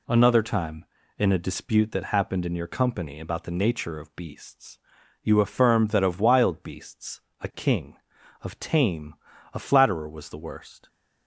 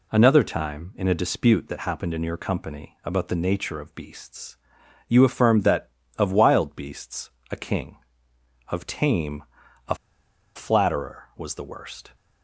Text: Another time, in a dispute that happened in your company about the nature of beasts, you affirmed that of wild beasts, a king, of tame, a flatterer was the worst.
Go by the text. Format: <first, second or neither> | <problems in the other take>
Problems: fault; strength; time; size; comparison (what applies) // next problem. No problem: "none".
first | pauses between "a" and "flatterer"; noticeable; at 9.9 s; 0.60 s long